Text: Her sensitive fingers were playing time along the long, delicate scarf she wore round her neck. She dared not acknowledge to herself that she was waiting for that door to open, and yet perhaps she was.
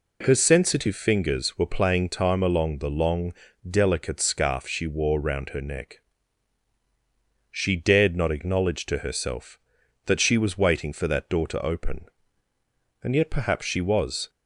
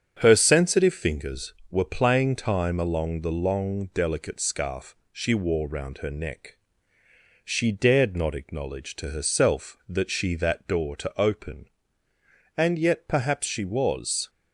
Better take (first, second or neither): first